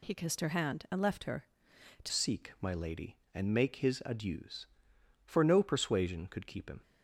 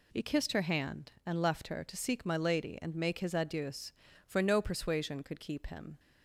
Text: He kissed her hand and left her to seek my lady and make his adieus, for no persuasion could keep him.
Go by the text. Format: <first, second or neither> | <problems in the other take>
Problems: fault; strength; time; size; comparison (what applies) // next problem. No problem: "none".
second | changes voice at "seek"; from 2.0 s on; 4.8 s long